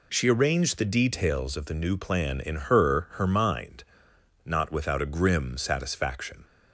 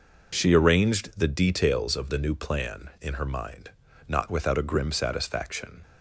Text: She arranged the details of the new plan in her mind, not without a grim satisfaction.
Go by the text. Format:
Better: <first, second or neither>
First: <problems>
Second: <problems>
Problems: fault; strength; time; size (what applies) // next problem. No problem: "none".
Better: second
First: says "her" twice; at 3.1 s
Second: none